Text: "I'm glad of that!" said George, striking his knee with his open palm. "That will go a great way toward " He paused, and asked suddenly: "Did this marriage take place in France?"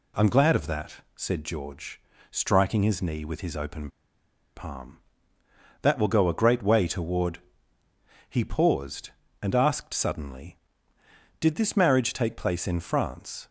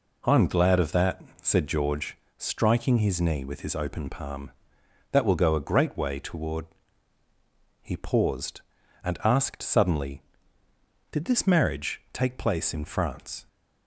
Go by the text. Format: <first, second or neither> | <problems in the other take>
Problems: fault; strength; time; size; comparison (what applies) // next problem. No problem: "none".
second | pauses between "open" and "palm"; noticeable; at 3.8 s; 0.67 s long